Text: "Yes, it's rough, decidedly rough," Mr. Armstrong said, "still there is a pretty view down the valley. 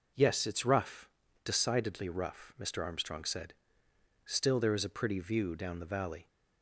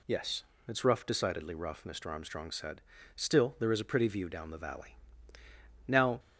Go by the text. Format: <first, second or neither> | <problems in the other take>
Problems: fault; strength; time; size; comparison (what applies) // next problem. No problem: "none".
first | goes on to say "Now"; slight; from 5.8 s on; 0.32 s long